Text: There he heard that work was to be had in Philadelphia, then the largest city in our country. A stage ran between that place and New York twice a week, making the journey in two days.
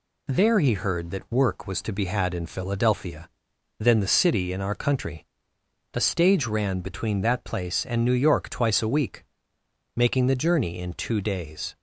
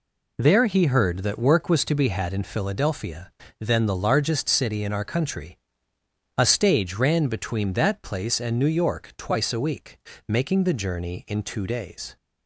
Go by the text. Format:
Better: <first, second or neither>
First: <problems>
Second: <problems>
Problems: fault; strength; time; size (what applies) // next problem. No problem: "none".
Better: second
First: skips "largest"; at 4.1 s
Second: none